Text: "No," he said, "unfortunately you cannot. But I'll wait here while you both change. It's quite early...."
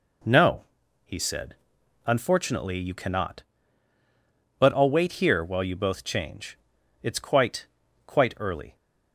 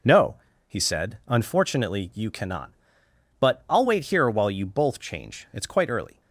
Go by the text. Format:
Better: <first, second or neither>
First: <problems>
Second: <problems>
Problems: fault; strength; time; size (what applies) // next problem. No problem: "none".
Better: second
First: says "quite" twice; at 8.0 s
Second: none